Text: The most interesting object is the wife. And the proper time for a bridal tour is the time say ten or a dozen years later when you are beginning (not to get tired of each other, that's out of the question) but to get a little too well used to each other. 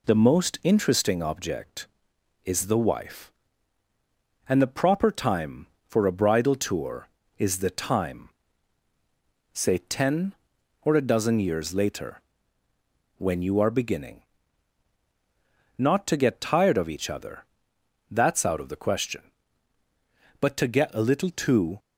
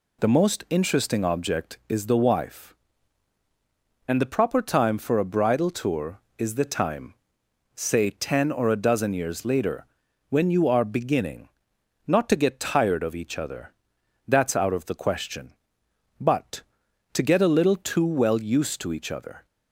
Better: second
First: pauses between "time" and "say"; strong; at 8.2 s; 1.2 s long // pauses between "later" and "when"; noticeable; at 12.2 s; 0.96 s long // stops before "well used to each other"; at 21.7 s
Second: pauses between "time" and "say"; noticeable; at 7.1 s; 0.62 s long // pauses between "later" and "when"; at 9.8 s; 0.44 s long

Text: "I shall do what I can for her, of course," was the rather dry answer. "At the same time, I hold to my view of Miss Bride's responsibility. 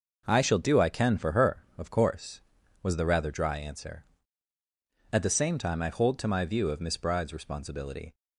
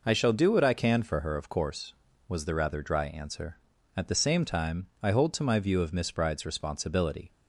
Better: second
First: skips "what"; at 0.8 s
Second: none

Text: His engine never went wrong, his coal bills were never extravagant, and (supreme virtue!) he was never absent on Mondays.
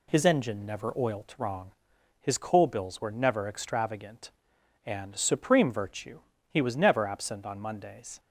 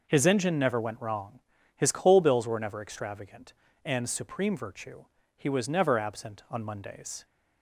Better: second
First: says "oilt" for "went"; at 0.9 s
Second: none

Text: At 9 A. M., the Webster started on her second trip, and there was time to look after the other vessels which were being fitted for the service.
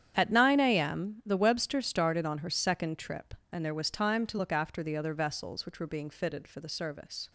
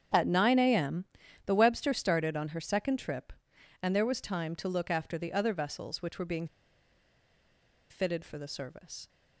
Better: first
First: starts louder than the rest; strong; until 1.2 s; 9 dB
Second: starts louder than the rest; strong; until 1.5 s; 8 dB // pauses between "being" and "fitted"; strong; at 6.4 s; 1.4 s long

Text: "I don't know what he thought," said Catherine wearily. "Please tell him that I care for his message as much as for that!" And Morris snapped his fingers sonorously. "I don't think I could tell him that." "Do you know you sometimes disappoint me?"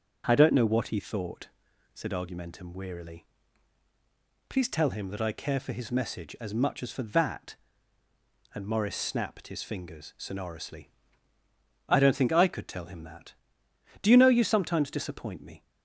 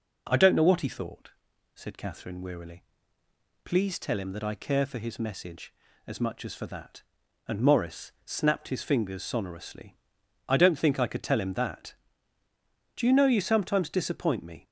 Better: second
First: starts louder than the rest; until 1.2 s; 6.5 dB // says "Argumentum" for "Catherine"; at 2.1 s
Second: none

